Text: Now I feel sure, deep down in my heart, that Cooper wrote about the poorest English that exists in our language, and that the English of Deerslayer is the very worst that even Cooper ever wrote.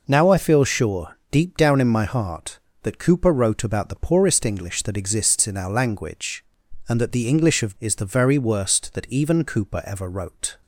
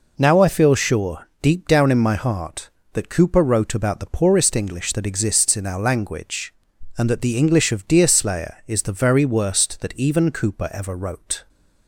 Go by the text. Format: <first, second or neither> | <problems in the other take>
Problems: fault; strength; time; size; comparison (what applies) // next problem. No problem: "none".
second | skips "Deerslayer"; at 7.7 s